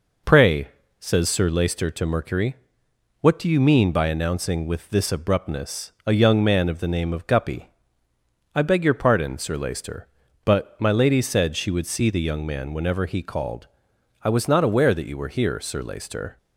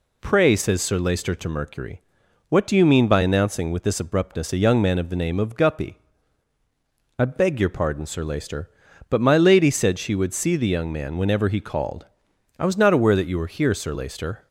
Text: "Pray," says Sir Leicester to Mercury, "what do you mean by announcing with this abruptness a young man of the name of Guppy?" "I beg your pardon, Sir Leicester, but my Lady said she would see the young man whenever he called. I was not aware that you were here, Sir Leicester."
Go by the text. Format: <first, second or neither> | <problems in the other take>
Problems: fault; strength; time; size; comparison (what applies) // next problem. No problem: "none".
neither | none